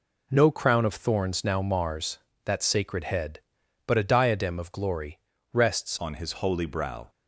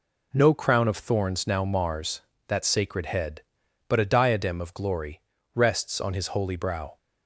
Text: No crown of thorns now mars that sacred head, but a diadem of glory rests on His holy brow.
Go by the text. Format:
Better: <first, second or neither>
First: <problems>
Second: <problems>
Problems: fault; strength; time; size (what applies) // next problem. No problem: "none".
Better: second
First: pauses between "glory" and "rests"; slight; at 5.1 s; 0.34 s long // changes voice at "on"; from 5.9 s on; 1.1 s long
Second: pauses between "glory" and "rests"; slight; at 5.2 s; 0.34 s long